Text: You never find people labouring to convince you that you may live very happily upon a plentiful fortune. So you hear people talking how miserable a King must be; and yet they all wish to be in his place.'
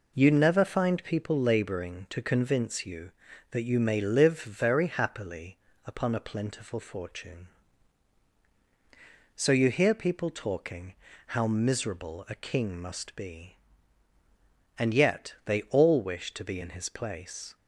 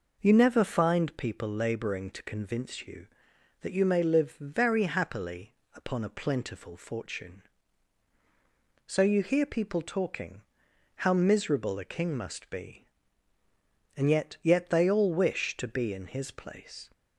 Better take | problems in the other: first | pauses between "happily" and "upon"; slight; at 5.5 s; 0.22 s long; slight in the first // pauses between "talking" and "how"; noticeable; at 10.4 s; 0.54 s long; slight in the first // says "yet" twice; at 14.4 s

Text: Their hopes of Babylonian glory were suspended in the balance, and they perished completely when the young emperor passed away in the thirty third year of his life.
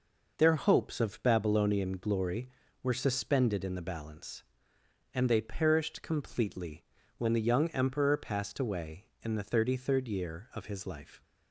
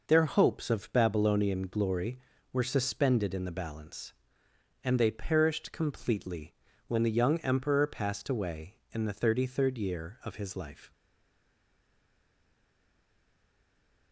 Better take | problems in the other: first | pauses between "completely" and "when"; slight; at 6.5 s; 0.34 s long; slight in the first // stays silent after the last word; strong; from 10.9 s on; 3.2 s long

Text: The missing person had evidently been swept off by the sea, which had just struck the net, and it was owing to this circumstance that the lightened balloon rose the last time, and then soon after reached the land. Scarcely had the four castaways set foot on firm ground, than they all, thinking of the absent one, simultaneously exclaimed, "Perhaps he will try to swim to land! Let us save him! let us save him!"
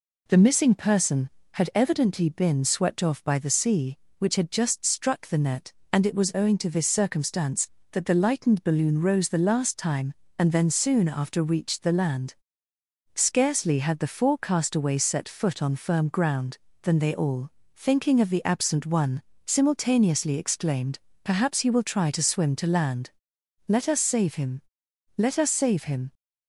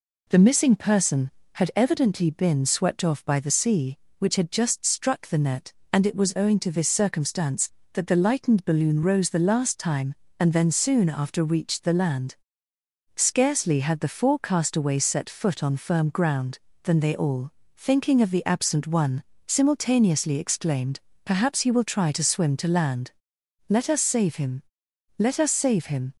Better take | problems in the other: neither | none

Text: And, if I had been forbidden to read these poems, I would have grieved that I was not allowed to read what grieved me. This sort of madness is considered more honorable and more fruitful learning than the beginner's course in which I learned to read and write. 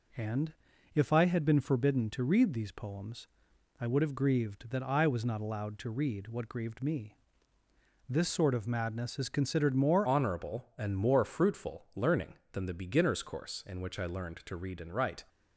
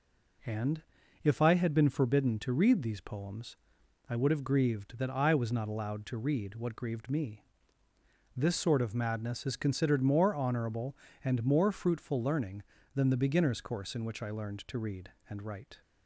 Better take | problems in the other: second | changes voice at "honorable"; from 10.0 s on; 5.2 s long

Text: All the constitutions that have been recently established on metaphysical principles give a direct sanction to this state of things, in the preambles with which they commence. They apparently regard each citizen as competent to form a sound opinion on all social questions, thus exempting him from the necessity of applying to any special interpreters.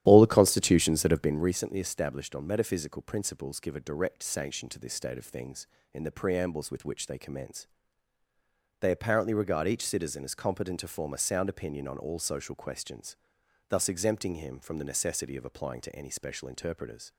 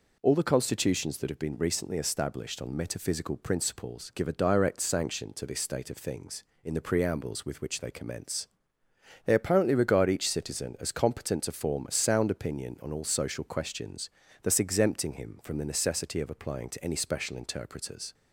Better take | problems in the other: second | starts louder than the rest; strong; until 1.5 s; 12 dB

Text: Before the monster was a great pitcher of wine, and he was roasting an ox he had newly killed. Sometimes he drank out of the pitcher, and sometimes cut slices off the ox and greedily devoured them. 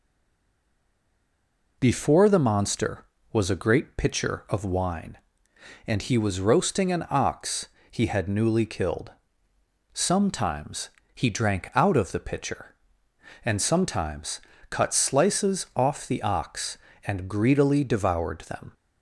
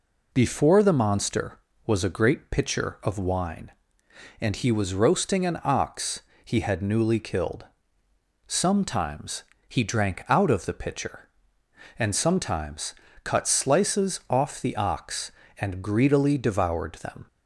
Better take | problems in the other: second | stays silent before the first word; noticeable; until 1.7 s; 1.7 s long // pauses between "ox" and "he"; slight; at 7.6 s; 0.20 s long; slight in the second // pauses between "Sometimes" and "he"; slight; at 10.8 s; 0.26 s long; slight in the second // pauses between "sometimes" and "cut"; slight; at 14.4 s; 0.28 s long; slight in the second

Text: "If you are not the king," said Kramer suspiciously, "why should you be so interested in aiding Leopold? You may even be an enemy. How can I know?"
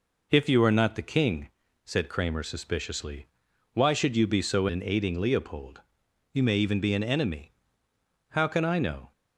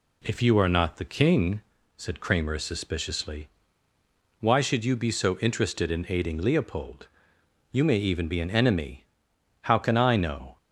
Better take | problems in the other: second | skips "interested"; at 4.6 s

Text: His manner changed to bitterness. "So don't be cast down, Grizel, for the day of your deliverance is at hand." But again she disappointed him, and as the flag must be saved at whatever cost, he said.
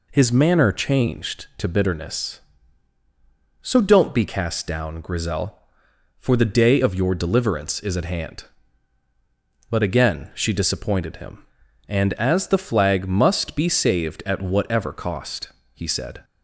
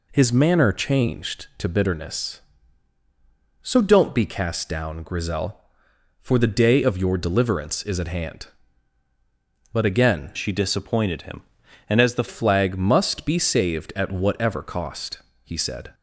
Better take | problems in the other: first | changes voice from "she" to "the"; from 10.3 to 12.2 s; 1.9 s long

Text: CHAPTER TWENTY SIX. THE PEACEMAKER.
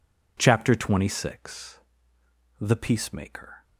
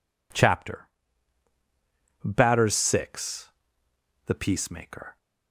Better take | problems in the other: first | says "Batters" for "TWENTY"; at 2.2 s

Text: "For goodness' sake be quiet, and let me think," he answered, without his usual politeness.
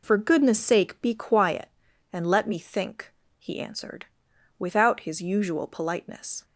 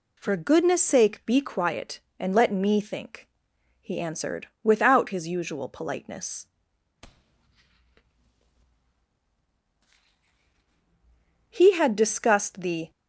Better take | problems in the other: first | goes on to say "He had discussed the"; from 11.5 s on; 1.4 s long

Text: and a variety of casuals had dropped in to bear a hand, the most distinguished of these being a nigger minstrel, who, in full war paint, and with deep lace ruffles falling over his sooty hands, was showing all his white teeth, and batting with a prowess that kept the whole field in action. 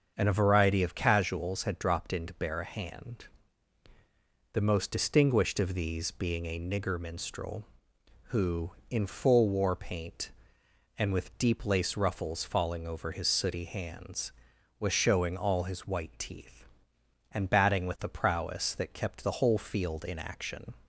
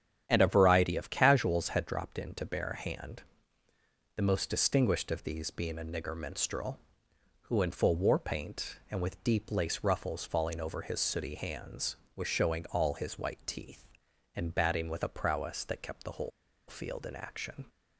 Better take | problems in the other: first | starts louder than the rest; strong; until 1.2 s; 9 dB; also in the first // pauses between "whole" and "field"; at 16.3 s; 0.39 s long

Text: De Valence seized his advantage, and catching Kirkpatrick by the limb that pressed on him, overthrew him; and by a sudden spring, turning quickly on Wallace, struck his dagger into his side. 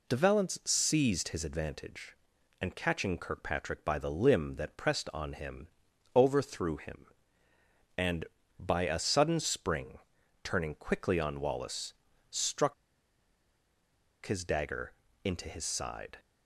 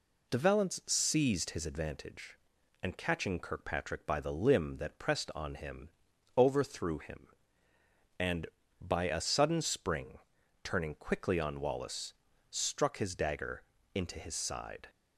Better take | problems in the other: second | pauses between "struck" and "his"; strong; at 12.7 s; 1.5 s long // pauses between "dagger" and "into"; slight; at 14.9 s; 0.28 s long; slight in the second

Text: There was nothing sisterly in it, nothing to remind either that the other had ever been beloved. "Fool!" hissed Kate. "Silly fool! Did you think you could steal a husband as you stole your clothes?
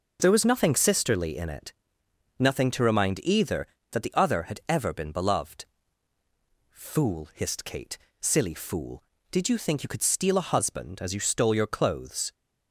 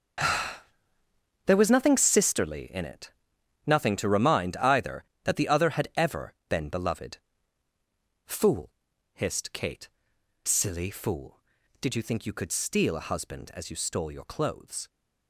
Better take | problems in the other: first | gets quieter; strong; throughout; 11 dB // pauses between "ever" and "been"; slight; at 6.3 s; 0.16 s long

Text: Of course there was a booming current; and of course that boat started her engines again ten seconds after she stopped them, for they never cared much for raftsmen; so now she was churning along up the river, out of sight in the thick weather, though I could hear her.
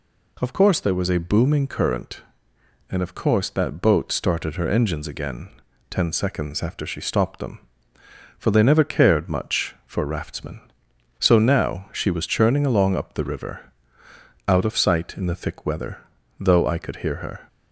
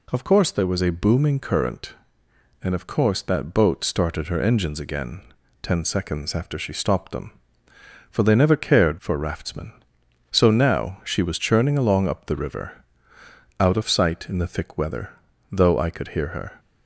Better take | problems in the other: first | pauses between "again" and "ten"; at 5.2 s; 0.42 s long; also in the first // skips "much"; at 8.9 s

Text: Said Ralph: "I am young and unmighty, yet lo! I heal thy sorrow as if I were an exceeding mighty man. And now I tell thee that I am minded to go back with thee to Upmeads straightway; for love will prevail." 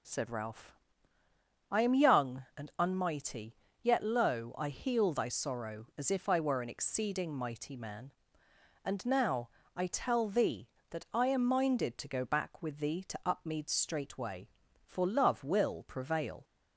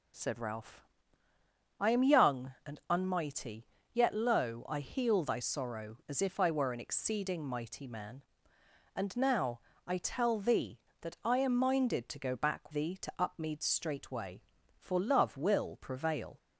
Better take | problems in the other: first | pauses between "now" and "I"; slight; at 9.5 s; 0.26 s long; slight in the first // skips "with"; at 12.7 s

